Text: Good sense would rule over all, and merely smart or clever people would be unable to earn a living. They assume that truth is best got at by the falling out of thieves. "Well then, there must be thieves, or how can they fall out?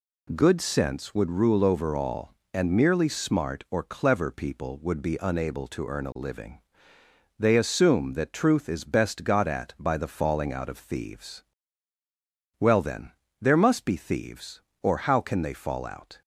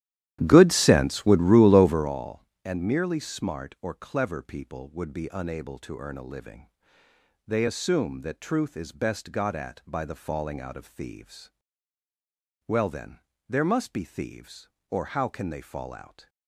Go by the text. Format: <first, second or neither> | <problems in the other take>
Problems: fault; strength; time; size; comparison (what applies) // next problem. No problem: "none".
first | starts louder than the rest; strong; until 2.2 s; 12.5 dB